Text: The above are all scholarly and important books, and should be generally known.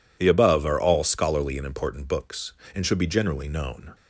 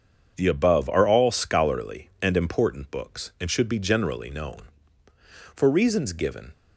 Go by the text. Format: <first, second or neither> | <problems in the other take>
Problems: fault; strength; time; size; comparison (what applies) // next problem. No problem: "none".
first | starts louder than the rest; until 1.3 s; 7 dB // goes on to say "For reasons given"; noticeable; from 5.5 s on; 0.98 s long